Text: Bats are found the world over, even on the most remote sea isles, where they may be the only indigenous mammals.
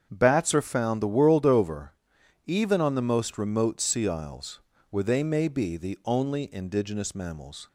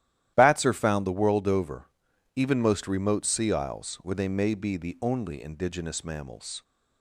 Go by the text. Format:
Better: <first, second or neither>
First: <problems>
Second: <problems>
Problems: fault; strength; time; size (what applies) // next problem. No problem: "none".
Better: first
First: starts louder than the rest; strong; until 1.1 s; 7.5 dB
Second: starts louder than the rest; strong; until 1.3 s; 13 dB // skips "on the"; at 2.6 s